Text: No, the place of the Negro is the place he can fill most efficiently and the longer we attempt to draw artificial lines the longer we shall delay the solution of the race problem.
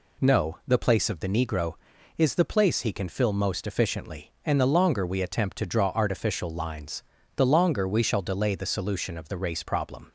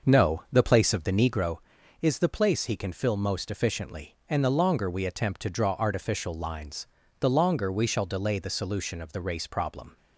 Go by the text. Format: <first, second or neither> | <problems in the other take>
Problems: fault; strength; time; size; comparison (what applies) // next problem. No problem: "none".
first | starts louder than the rest; noticeable; until 1.5 s; 6 dB // pauses between "lines" and "the"; slight; at 6.8 s; 0.34 s long; slight in the first